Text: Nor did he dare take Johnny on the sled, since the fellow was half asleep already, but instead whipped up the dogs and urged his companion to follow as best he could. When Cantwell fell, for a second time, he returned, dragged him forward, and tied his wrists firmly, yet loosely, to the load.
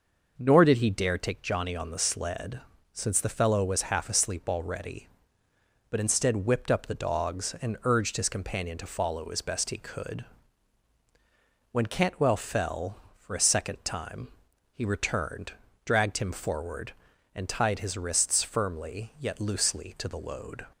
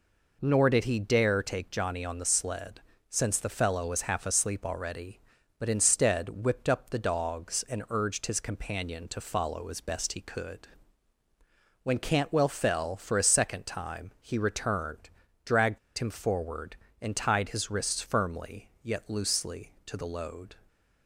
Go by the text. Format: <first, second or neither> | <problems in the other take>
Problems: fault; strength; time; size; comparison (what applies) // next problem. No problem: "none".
first | pauses between "dragged" and "him"; slight; at 15.7 s; 0.20 s long